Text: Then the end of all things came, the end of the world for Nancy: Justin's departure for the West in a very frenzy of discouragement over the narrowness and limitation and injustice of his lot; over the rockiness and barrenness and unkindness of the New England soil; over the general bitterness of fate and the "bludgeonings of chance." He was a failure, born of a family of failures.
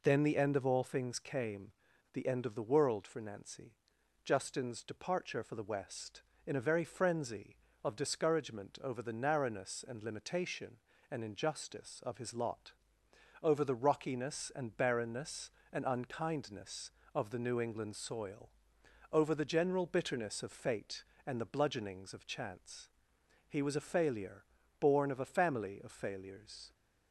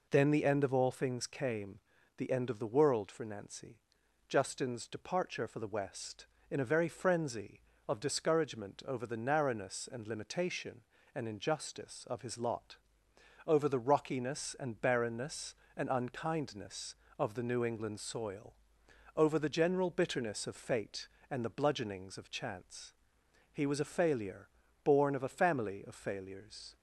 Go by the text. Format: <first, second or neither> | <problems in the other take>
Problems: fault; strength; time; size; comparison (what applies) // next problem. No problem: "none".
neither | none